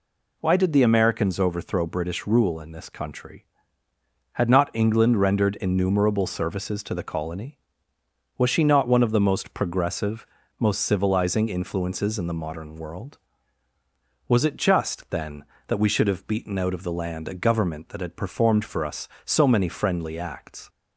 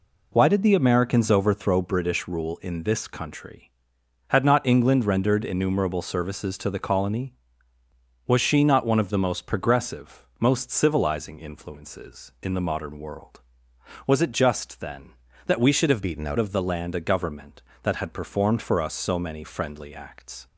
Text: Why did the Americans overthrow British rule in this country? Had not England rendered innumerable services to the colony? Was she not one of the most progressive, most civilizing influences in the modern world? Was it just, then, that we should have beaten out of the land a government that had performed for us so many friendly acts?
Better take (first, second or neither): first